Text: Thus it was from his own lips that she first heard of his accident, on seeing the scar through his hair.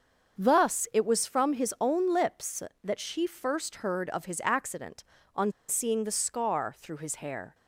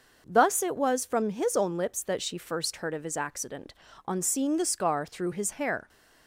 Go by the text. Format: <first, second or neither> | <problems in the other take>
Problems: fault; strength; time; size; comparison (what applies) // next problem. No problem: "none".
second | starts louder than the rest; until 1.4 s; 6.5 dB; noticeable in the second // pauses between "on" and "seeing"; slight; at 5.5 s; 0.16 s long